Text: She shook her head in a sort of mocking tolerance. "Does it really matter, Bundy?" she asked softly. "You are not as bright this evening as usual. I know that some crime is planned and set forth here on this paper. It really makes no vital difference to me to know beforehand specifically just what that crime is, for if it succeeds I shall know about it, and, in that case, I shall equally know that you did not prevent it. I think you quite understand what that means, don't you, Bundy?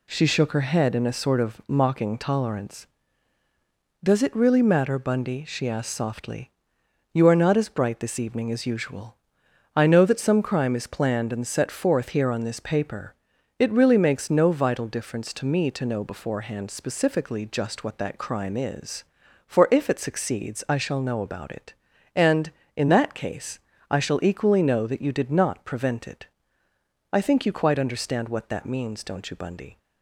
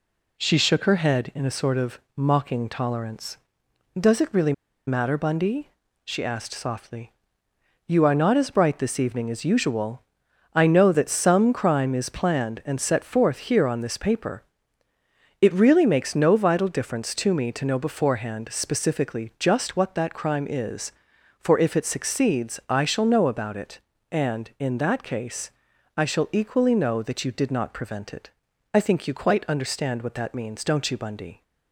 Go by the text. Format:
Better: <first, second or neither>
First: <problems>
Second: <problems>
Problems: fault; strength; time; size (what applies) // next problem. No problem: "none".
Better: first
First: none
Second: pauses between "of" and "mocking"; slight; at 1.9 s; 0.18 s long // pauses between "really" and "matter"; slight; at 4.5 s; 0.34 s long